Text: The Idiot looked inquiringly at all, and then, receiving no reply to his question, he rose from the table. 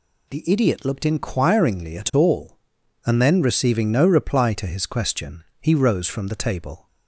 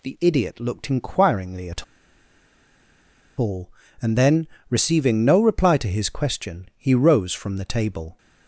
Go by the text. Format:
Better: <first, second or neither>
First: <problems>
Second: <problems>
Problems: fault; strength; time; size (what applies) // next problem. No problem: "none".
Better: first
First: none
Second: pauses between "at" and "all"; strong; at 1.8 s; 1.5 s long